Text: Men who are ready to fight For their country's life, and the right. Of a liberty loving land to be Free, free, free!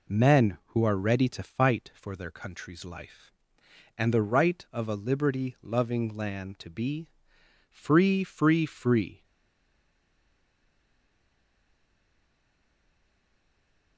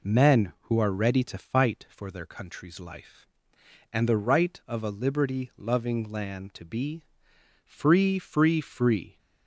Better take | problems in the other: second | pauses between "be" and "Free"; noticeable; at 7.0 s; 0.60 s long; noticeable in the second // stays silent after the last word; strong; from 9.2 s on; 4.7 s long

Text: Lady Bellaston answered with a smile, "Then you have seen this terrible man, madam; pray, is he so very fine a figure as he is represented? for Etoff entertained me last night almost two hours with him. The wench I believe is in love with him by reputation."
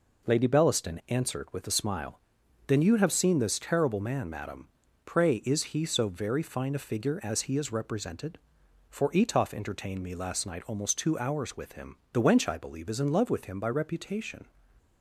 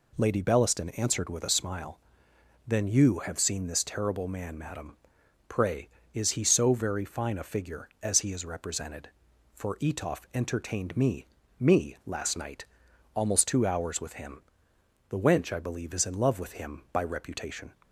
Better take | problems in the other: first | says "me" twice; at 11.5 s // pauses between "night" and "almost"; noticeable; at 12.6 s; 0.48 s long

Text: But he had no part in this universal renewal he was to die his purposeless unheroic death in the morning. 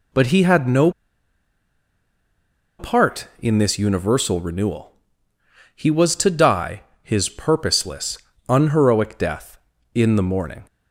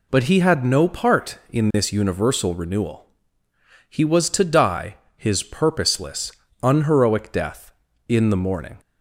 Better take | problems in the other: second | pauses between "no" and "part"; strong; at 0.8 s; 1.8 s long // pauses between "renewal" and "he"; noticeable; at 4.9 s; 0.86 s long; noticeable in the second // pauses between "die" and "his"; slight; at 6.8 s; 0.20 s long; slight in the second // pauses between "purposeless" and "unheroic"; slight; at 8.1 s; 0.30 s long; slight in the second

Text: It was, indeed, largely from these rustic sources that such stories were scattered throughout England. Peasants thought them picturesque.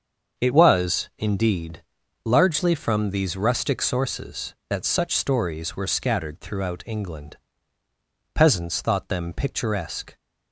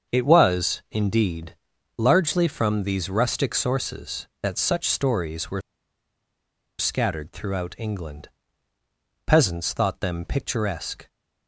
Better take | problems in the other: first | starts louder than the rest; until 1.1 s; 6.5 dB; also in the first // pauses between "were" and "scattered"; at 5.5 s; 1.1 s long

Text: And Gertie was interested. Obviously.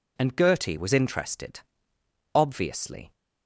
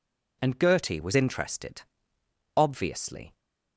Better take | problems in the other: neither | none

